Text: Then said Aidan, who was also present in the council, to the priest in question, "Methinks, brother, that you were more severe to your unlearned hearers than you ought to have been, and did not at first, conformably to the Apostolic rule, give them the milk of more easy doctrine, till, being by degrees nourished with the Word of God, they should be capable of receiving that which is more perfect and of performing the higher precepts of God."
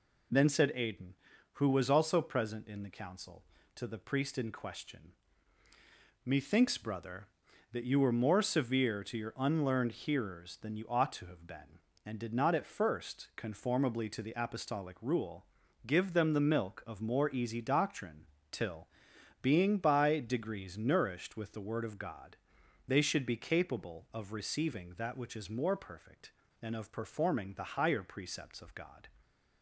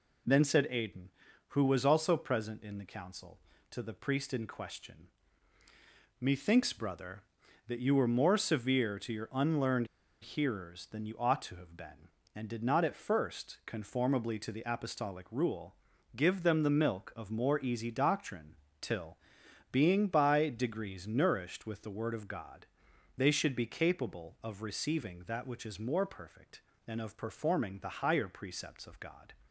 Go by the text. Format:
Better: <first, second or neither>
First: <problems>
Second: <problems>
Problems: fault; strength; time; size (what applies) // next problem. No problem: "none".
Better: first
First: none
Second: pauses between "unlearned" and "hearers"; slight; at 9.8 s; 0.35 s long